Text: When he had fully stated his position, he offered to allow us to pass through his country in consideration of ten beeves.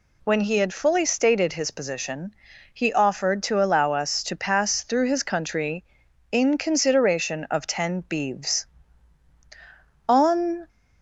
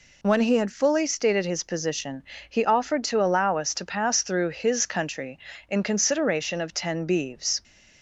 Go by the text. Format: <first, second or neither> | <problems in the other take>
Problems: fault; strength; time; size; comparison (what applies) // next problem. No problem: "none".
second | goes on to say "On"; noticeable; from 10.0 s on; 0.62 s long